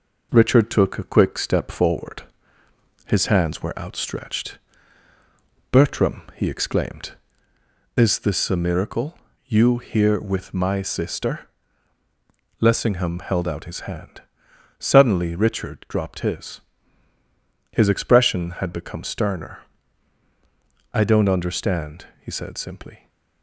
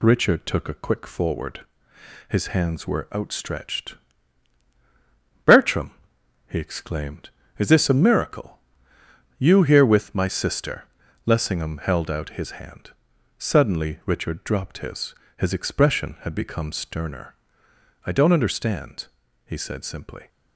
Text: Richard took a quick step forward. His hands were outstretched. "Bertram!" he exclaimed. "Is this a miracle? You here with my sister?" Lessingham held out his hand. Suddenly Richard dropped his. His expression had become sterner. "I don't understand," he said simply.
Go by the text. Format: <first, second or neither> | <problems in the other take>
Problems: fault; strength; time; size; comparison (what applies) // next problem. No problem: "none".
first | skips "step"; at 1.0 s